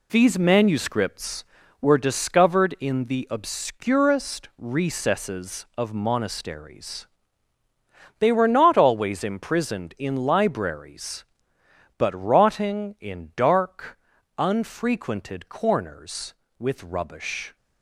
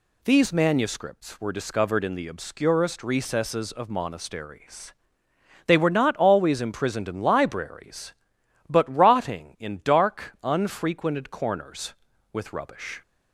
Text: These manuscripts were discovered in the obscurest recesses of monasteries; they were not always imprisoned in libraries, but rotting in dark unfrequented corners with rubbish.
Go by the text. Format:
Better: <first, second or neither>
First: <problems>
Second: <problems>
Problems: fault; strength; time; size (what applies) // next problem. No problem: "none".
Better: second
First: gets quieter; throughout; 7 dB // pauses between "dark" and "unfrequented"; at 13.9 s; 0.40 s long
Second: none